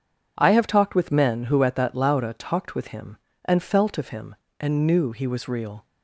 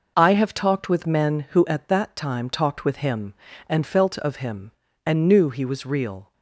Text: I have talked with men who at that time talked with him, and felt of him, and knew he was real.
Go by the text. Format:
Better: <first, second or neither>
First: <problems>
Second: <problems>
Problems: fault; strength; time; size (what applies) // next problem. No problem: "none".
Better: second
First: says "lauda" for "time"; at 1.9 s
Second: none